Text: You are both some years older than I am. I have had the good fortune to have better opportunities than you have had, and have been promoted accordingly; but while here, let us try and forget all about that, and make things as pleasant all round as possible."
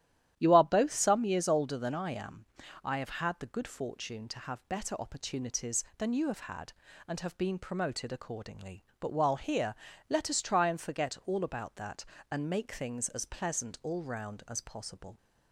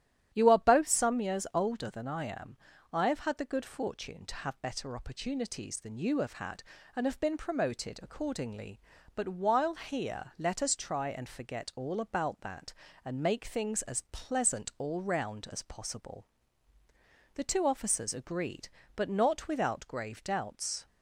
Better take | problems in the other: first | starts louder than the rest; strong; until 1.3 s; 11 dB; strong in the first // goes on to say "The two officers agreed but not without grave doubts"; strong; from 17.3 s on; 3.5 s long

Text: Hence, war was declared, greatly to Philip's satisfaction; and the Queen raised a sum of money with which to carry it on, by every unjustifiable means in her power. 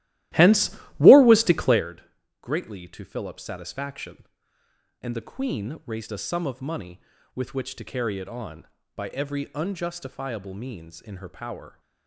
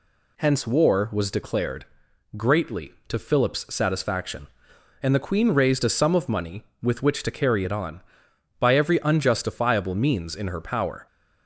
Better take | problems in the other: second | starts louder than the rest; strong; until 1.8 s; 15.5 dB

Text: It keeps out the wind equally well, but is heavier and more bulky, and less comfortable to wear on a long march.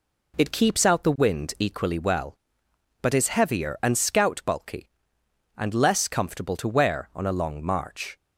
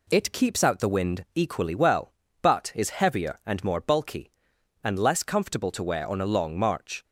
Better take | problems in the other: second | says "scout" for "more"; at 3.9 s

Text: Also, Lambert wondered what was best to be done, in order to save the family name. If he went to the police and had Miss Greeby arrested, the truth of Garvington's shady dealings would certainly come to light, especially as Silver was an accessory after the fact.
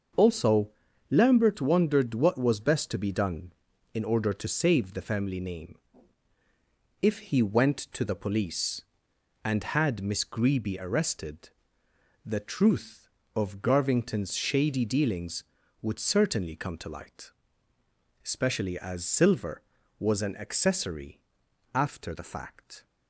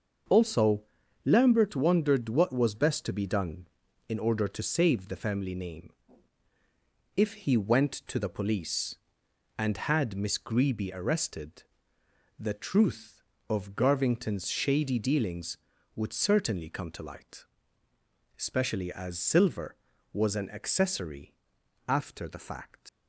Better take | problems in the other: first | starts louder than the rest; until 1.7 s; 6 dB; also in the first // pauses between "accessory" and "after"; noticeable; at 21.3 s; 0.56 s long; noticeable in the first // leaves "fact" unfinished; at 22.8 s; 110 ms

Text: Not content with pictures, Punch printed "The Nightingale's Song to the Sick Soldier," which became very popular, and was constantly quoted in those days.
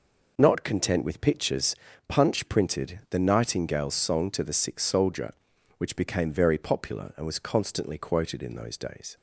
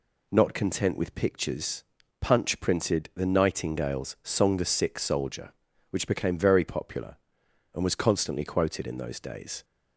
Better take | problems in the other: first | skips "to"; at 4.5 s

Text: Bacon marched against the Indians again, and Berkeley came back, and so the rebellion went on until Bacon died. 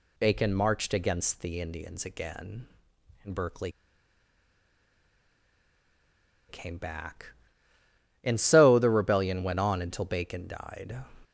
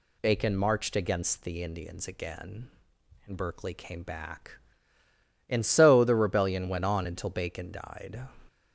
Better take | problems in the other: second | pauses between "Berkeley" and "came"; strong; at 3.7 s; 2.7 s long

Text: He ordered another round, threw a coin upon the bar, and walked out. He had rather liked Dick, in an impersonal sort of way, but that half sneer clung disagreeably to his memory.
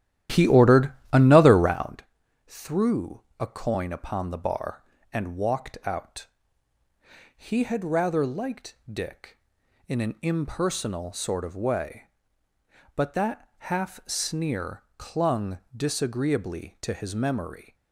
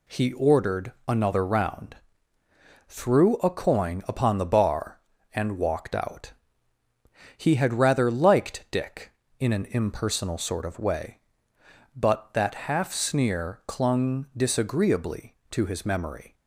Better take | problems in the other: second | starts louder than the rest; strong; until 2.0 s; 12.5 dB // pauses between "ordered" and "another"; slight; at 0.9 s; 0.20 s long // pauses between "threw" and "a"; slight; at 3.1 s; 0.22 s long // pauses between "that" and "half"; slight; at 13.4 s; 0.18 s long // pauses between "clung" and "disagreeably"; slight; at 15.5 s; 0.16 s long

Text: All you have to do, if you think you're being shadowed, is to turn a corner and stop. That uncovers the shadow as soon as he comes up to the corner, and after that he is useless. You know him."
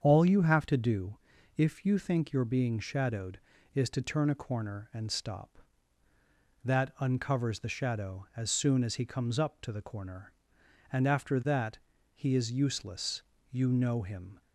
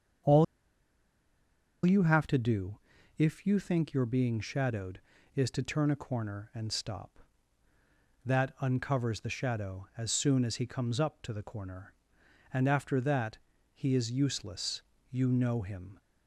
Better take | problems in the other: first | starts louder than the rest; strong; until 2.6 s; 7.5 dB; strong in the first // pauses between "All" and "you"; strong; at 0.4 s; 1.4 s long // pauses between "that" and "he"; slight; at 13.3 s; 0.36 s long; slight in the first

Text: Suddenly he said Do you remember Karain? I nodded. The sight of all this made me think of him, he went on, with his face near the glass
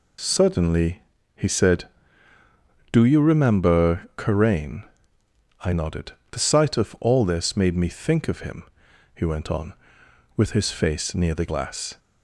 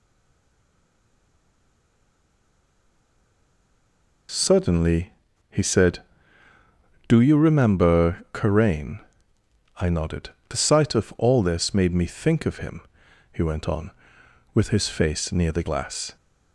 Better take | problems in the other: first | stays silent before the first word; strong; until 4.2 s; 4.2 s long // pauses between "Suddenly" and "he"; at 5.0 s; 0.37 s long; slight in the first

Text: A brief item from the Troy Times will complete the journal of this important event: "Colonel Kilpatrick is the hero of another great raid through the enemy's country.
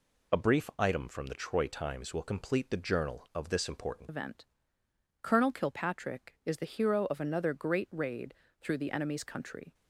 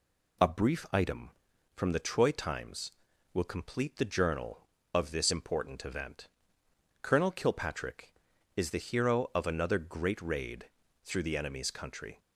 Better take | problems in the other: second | changes voice at "event"; from 4.0 s on; 5.7 s long // pauses between "raid" and "through"; slight; at 8.3 s; 0.30 s long; slight in the second

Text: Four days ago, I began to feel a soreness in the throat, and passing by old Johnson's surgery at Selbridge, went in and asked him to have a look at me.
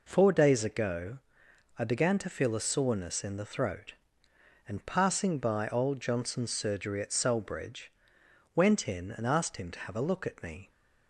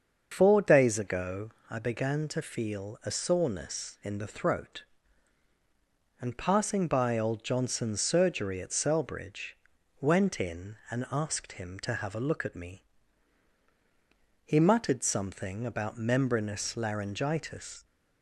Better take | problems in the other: first | starts louder than the rest; until 1.3 s; 6.5 dB // goes on to say "He muttered something about membranous laryngitis"; strong; from 14.4 s on; 3.3 s long

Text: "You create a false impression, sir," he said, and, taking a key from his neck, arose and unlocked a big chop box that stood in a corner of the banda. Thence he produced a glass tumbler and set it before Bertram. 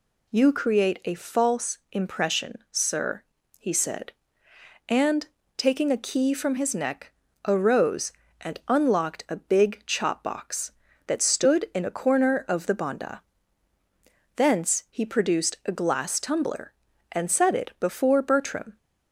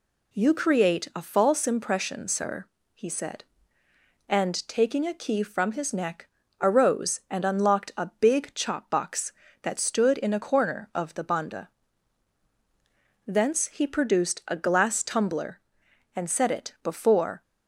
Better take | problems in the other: first | stops before "Bertram"; at 17.4 s

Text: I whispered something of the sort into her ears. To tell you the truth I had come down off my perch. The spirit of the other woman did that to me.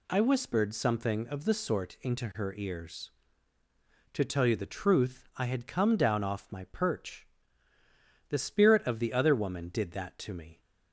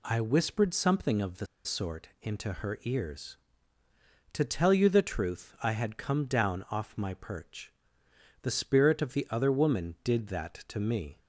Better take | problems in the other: first | pauses between "the" and "sort"; slight; at 1.4 s; 0.18 s long

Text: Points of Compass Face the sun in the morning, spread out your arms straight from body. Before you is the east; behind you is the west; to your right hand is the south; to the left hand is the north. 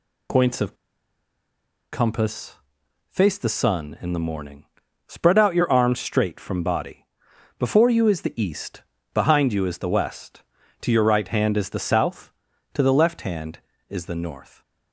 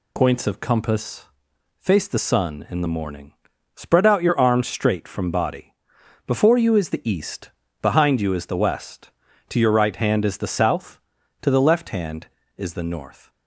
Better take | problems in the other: second | pauses between "of" and "Compass"; at 0.7 s; 1.1 s long // pauses between "Compass" and "Face"; noticeable; at 2.5 s; 0.52 s long; noticeable in the second

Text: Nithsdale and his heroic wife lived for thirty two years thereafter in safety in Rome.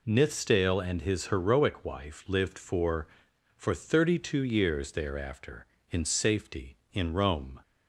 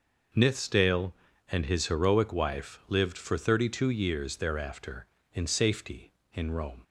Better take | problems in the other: second | says "for" twice; at 3.5 s

